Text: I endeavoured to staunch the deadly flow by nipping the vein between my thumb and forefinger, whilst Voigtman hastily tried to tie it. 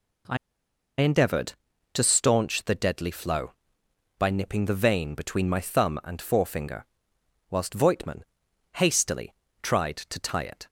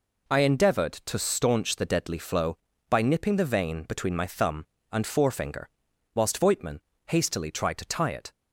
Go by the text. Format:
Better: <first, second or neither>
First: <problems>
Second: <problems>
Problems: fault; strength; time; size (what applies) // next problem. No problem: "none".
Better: second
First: pauses between "I" and "endeavoured"; noticeable; at 0.3 s; 0.63 s long // pauses between "Voigtman" and "hastily"; noticeable; at 8.2 s; 0.54 s long // pauses between "hastily" and "tried"; slight; at 9.3 s; 0.26 s long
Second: pauses between "Voigtman" and "hastily"; slight; at 6.8 s; 0.25 s long